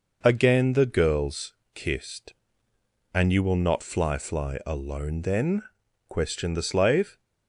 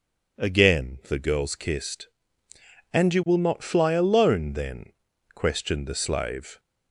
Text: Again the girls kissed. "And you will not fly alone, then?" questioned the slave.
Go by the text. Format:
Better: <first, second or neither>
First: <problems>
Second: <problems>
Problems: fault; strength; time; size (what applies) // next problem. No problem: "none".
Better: second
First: pauses between "girls" and "kissed"; slight; at 1.5 s; 0.18 s long // says "fly" twice; at 4.1 s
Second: none